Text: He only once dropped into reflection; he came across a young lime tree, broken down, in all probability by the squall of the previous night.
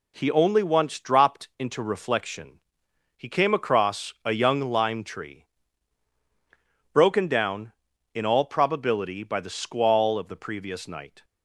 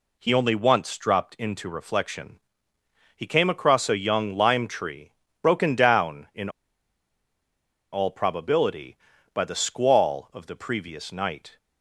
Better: first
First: none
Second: pauses between "in" and "all"; strong; at 6.5 s; 1.4 s long

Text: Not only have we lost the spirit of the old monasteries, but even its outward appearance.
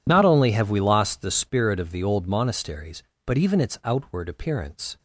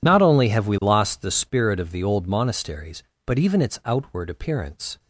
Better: neither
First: none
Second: none

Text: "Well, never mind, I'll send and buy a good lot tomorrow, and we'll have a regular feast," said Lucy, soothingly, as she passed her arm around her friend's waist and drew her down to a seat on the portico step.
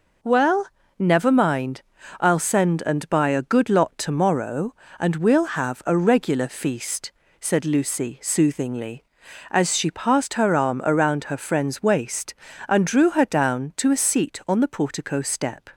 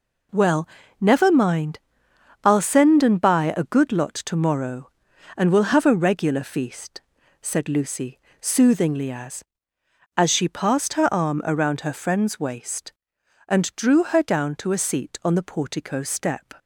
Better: first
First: none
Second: says "as" twice; at 10.1 s

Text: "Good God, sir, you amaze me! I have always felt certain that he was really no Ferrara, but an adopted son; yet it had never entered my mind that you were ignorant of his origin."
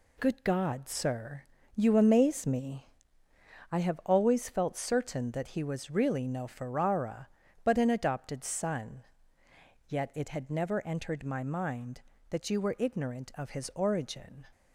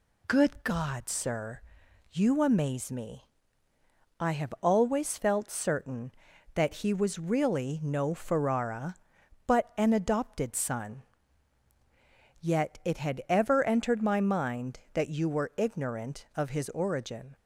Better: first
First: none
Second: says "ever" for "never"; at 13.2 s

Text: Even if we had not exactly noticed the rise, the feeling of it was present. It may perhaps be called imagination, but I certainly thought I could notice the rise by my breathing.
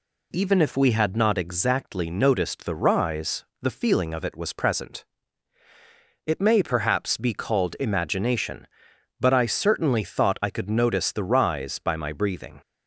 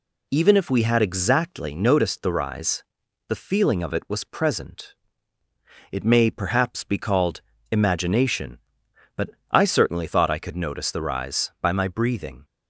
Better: first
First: none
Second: skips "not"; at 1.0 s // pauses between "called" and "imagination"; slight; at 7.4 s; 0.28 s long // pauses between "but" and "I"; slight; at 9.3 s; 0.22 s long

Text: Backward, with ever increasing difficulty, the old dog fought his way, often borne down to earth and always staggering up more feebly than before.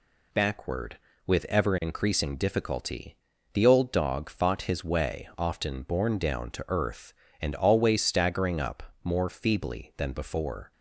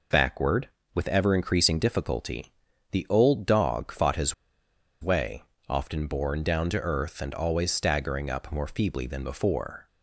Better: first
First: none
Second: pauses between "his" and "way"; noticeable; at 4.3 s; 0.68 s long

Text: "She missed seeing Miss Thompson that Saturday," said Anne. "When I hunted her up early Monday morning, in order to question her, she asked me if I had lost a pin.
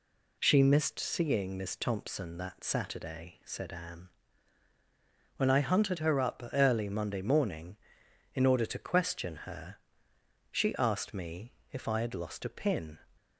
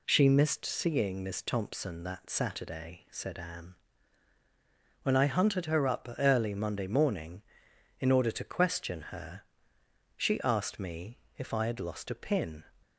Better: neither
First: pauses between "me" and "if"; slight; at 11.5 s; 0.20 s long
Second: pauses between "me" and "if"; slight; at 11.1 s; 0.20 s long

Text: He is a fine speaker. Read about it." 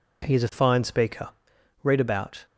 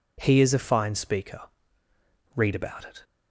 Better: second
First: stops before "it"; at 2.4 s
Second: none

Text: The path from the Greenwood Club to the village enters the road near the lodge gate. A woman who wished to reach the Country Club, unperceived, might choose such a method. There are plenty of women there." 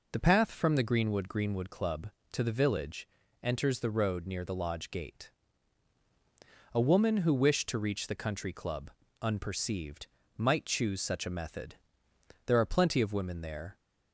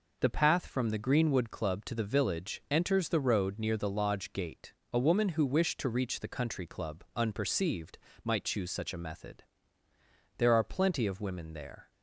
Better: second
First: says "Greenwood" twice; at 1.2 s // pauses between "village" and "enters"; at 3.0 s; 0.38 s long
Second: none

